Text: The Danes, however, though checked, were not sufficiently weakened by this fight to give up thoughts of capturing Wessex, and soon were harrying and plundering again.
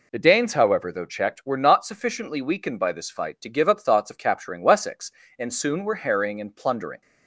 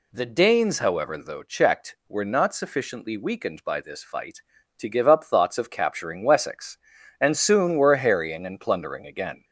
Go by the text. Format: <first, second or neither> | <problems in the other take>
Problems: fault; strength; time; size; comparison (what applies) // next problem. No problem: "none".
second | stops before "again"; at 7.0 s